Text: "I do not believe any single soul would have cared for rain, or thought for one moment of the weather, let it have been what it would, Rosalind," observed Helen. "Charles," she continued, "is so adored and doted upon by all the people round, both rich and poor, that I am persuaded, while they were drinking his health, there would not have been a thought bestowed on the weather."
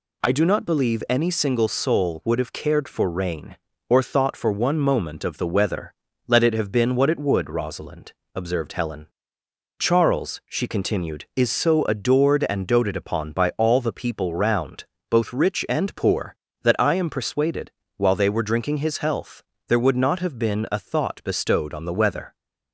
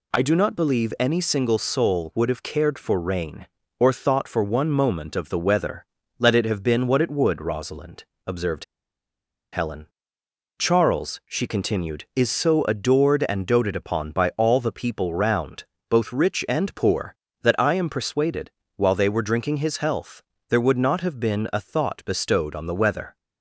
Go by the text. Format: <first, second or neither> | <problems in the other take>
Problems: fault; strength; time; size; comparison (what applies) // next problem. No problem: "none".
first | pauses between "observed" and "Helen"; noticeable; at 8.6 s; 0.88 s long